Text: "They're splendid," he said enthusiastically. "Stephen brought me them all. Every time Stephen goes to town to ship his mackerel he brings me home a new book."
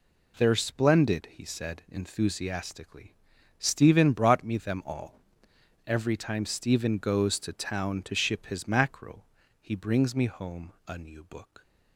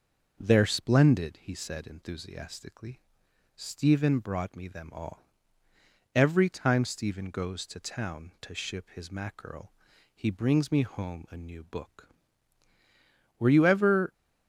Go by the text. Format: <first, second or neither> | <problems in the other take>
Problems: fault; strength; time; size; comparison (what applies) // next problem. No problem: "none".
first | starts louder than the rest; noticeable; until 1.4 s; 6 dB // pauses between "mackerel" and "he"; at 9.7 s; 0.42 s long; slight in the first // goes on to say "Were you ever"; noticeable; from 13.3 s on; 0.76 s long